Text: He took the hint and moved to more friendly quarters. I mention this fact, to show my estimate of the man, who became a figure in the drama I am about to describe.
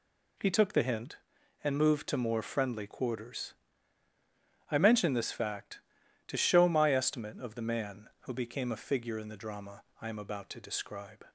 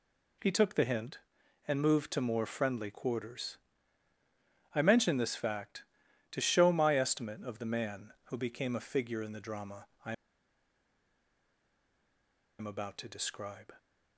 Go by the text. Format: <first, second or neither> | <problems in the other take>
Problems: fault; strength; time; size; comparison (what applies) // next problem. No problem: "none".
first | pauses between "drama" and "I"; slight; at 9.8 s; 0.18 s long; slight in the first // pauses between "I" and "am"; strong; at 10.1 s; 2.4 s long